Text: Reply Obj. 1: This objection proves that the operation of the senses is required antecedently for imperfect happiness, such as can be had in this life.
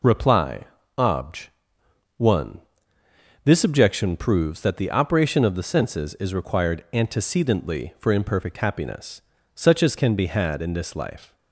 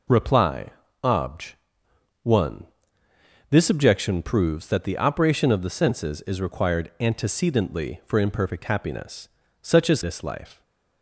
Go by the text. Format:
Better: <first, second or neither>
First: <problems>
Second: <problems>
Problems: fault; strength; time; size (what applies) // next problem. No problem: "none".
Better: first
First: pauses between "Reply" and "Obj"; slight; at 0.6 s; 0.34 s long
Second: pauses between "Reply" and "Obj"; slight; at 0.6 s; 0.34 s long // skips "can be had in"; at 10.0 s